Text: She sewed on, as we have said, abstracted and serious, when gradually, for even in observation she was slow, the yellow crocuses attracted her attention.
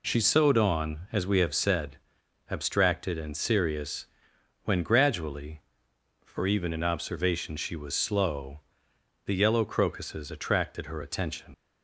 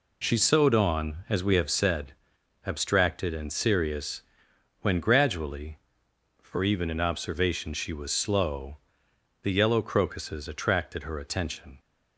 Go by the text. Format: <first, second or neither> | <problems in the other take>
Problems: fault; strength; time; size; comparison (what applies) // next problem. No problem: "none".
second | leaves "attention" unfinished; at 11.5 s; 70 ms